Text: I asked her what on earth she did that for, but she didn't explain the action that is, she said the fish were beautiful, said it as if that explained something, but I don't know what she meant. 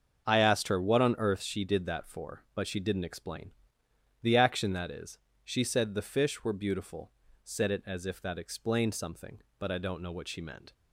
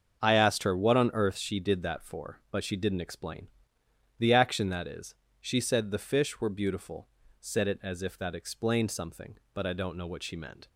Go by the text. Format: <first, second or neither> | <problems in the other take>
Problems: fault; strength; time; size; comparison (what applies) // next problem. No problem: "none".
neither | starts louder than the rest; the same in both // pauses between "explain" and "the"; noticeable; the same in both